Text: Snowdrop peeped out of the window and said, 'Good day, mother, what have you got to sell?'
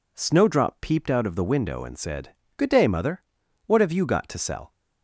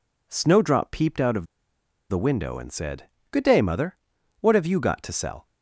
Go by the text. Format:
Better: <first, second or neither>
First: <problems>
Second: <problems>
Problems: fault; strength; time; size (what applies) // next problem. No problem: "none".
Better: first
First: none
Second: pauses between "of" and "the"; noticeable; at 1.4 s; 0.64 s long